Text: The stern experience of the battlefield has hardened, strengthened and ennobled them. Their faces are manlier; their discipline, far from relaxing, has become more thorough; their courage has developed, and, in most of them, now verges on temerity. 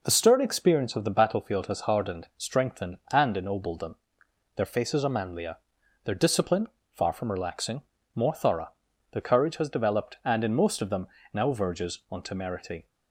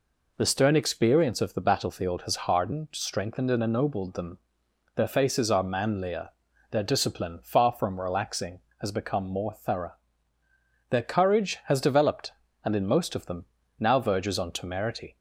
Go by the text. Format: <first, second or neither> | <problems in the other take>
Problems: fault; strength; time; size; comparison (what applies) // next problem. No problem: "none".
second | skips "has become"; at 7.9 s